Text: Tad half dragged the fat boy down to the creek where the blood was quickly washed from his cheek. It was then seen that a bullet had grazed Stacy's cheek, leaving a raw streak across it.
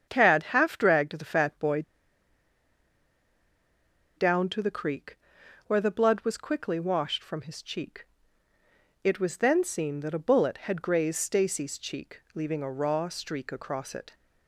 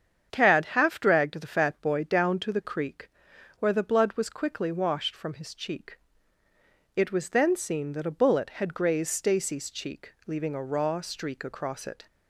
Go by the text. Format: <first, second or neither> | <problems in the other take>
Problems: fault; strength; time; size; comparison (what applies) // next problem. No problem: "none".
second | starts louder than the rest; strong; until 1.1 s; 7.5 dB; strong in the second // pauses between "boy" and "down"; strong; at 1.8 s; 2.3 s long // pauses between "creek" and "where"; noticeable; at 5.1 s; 0.48 s long; noticeable in the second